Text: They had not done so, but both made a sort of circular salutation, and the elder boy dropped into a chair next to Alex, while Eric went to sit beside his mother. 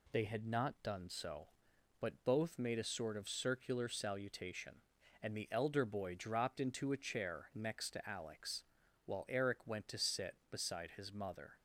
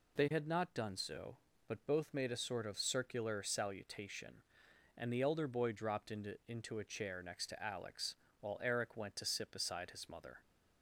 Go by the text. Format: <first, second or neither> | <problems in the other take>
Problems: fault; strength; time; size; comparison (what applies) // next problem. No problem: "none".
first | says "into" twice; at 6.4 s